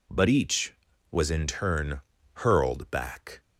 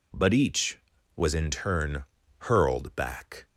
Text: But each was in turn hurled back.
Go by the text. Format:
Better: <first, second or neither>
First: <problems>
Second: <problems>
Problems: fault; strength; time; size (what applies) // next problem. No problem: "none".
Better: neither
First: pauses between "turn" and "hurled"; slight; at 2.0 s; 0.32 s long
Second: pauses between "turn" and "hurled"; slight; at 2.0 s; 0.34 s long